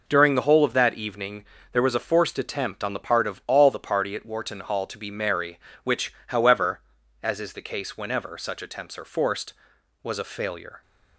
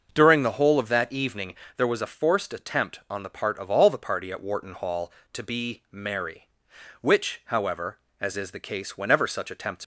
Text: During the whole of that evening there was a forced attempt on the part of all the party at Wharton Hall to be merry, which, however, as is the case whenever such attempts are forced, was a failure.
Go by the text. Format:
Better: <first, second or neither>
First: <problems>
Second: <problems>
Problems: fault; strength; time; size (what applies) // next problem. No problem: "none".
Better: first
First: pauses between "evening" and "there"; slight; at 1.4 s; 0.26 s long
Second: starts louder than the rest; noticeable; until 1.1 s; 6 dB // pauses between "evening" and "there"; slight; at 1.5 s; 0.22 s long // stops before "are forced was a failure"; at 9.8 s